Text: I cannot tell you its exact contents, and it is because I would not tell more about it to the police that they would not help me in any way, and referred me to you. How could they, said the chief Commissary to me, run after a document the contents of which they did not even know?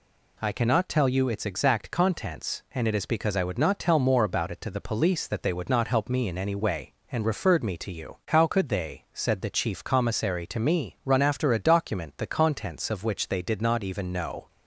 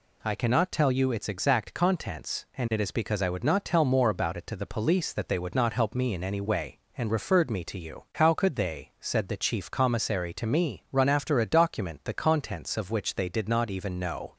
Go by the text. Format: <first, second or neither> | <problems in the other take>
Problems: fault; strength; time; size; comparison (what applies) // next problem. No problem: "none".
neither | none